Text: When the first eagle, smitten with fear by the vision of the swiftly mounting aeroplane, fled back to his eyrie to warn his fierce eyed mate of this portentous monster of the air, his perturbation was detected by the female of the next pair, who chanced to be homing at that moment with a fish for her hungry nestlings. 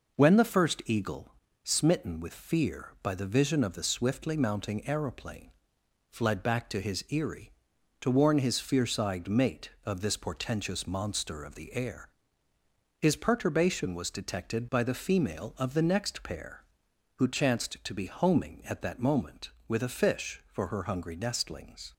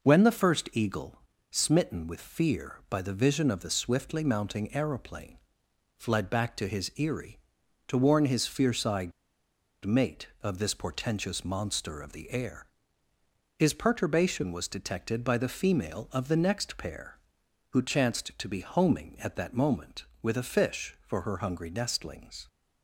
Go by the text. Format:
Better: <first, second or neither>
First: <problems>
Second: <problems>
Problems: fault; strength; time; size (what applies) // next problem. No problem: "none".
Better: first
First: none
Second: pauses between "eyed" and "mate"; noticeable; at 9.1 s; 0.73 s long